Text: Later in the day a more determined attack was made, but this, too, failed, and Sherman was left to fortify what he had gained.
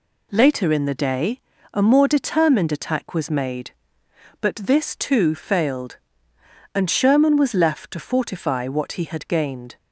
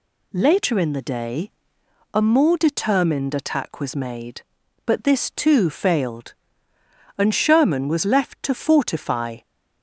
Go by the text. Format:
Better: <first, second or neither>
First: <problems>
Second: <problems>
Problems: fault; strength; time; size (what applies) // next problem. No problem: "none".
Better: first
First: pauses between "day" and "a"; slight; at 1.4 s; 0.32 s long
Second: pauses between "day" and "a"; noticeable; at 1.5 s; 0.62 s long // stops before "what he had gained"; at 9.4 s